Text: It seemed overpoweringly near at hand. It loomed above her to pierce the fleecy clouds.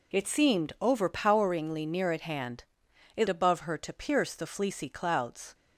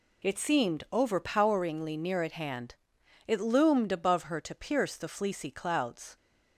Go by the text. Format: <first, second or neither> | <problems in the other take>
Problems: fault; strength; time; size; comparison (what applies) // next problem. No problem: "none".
second | skips "loomed"; at 3.2 s